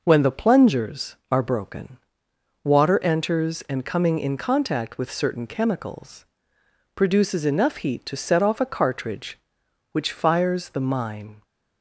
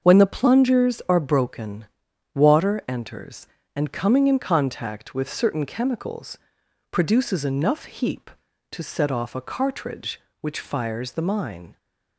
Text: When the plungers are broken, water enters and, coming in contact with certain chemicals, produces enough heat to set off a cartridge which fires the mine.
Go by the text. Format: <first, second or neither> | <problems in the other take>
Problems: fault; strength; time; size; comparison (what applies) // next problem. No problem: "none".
first | starts louder than the rest; until 1.1 s; 6.5 dB // says "heap" for "heat"; at 7.8 s